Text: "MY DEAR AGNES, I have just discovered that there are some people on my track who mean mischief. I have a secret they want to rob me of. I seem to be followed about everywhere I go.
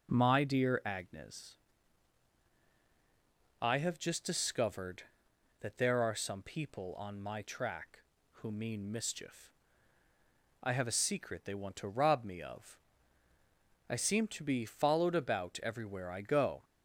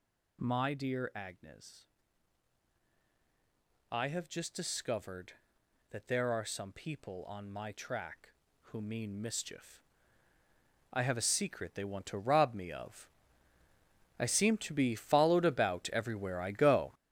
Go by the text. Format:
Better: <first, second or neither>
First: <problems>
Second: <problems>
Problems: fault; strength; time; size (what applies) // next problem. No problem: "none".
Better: first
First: none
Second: gets louder; strong; throughout; 9 dB